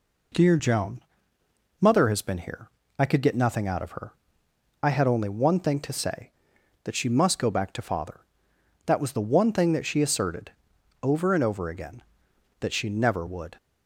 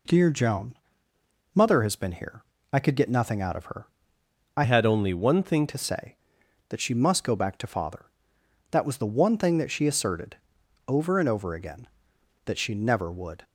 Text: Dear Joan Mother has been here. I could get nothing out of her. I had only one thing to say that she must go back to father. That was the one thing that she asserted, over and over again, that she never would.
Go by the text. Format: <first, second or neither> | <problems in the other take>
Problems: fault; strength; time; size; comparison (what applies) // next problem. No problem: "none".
first | pauses between "Joan" and "Mother"; noticeable; at 0.7 s; 0.76 s long; noticeable in the first // changes voice from "had" to "thing"; from 4.6 to 5.6 s; 1.0 s long